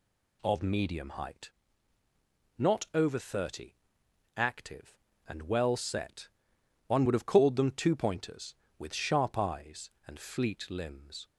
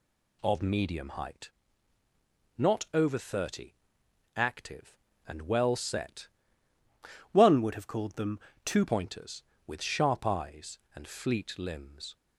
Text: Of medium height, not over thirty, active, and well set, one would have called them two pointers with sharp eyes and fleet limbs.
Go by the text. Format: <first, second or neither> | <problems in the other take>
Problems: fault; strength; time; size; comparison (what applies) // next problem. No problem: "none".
first | changes voice from "one" to "two"; from 7.3 to 8.8 s; 1.5 s long // pauses between "them" and "two"; slight; at 8.3 s; 0.28 s long